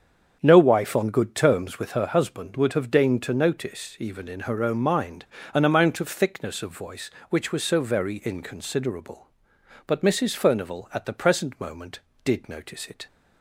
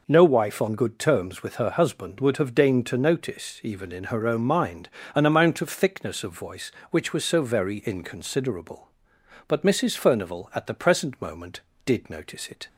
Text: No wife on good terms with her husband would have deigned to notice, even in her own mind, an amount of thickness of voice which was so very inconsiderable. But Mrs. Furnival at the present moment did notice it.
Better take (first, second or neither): second